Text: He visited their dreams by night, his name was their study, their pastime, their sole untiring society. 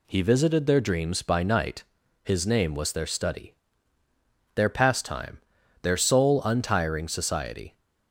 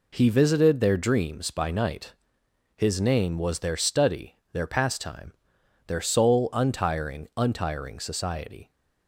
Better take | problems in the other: first | says "untiring" twice; at 7.3 s

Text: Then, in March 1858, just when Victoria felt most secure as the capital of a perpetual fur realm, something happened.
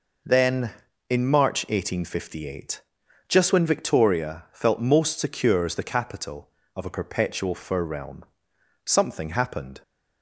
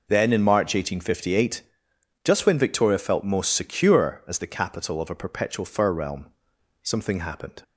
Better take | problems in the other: neither | none

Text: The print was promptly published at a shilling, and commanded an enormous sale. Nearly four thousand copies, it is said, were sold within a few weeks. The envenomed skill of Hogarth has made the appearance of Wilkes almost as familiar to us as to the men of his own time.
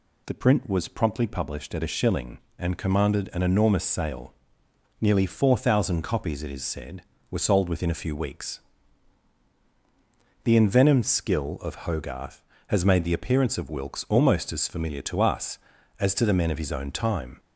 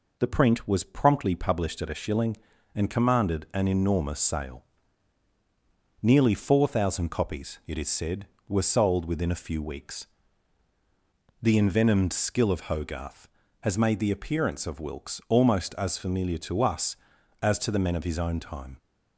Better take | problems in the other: neither | none

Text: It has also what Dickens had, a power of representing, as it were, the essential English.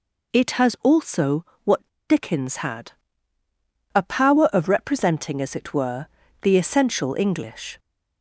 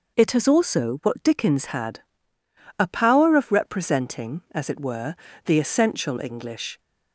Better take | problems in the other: second | pauses between "also" and "what"; slight; at 1.4 s; 0.20 s long // pauses between "what" and "Dickens"; slight; at 1.8 s; 0.28 s long

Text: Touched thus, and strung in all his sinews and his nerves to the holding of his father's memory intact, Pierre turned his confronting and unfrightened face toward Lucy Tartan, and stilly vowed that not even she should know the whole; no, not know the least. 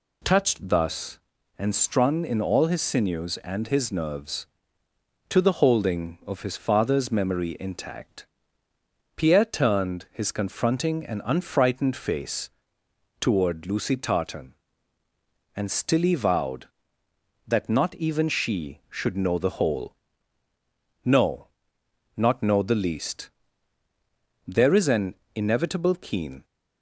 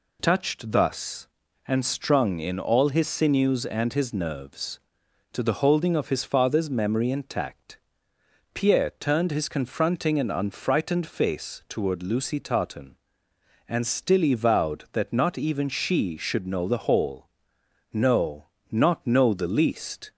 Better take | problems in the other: second | pauses between "face" and "toward"; noticeable; at 12.5 s; 0.68 s long // goes on to say "There is an inevitable keen"; strong; from 24.4 s on; 1.9 s long

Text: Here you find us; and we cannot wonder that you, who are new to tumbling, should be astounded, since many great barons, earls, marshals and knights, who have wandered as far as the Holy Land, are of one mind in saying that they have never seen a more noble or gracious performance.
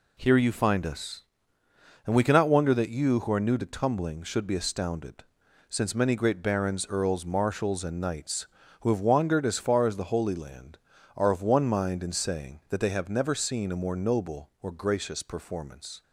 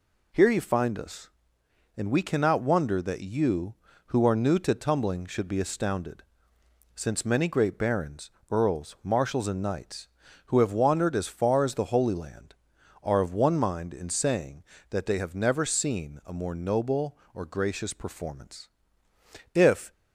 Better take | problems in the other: first | goes on to say "If"; slight; from 19.5 s on; 0.38 s long

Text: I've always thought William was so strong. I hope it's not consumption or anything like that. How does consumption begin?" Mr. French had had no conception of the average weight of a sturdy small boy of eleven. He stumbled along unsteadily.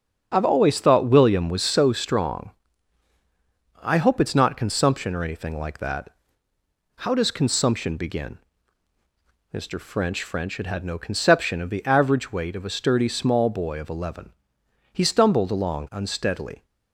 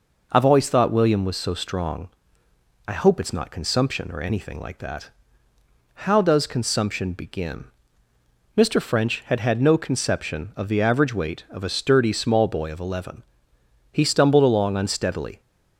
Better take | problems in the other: second | starts louder than the rest; strong; until 1.3 s; 7.5 dB // says "French" twice; at 10.2 s

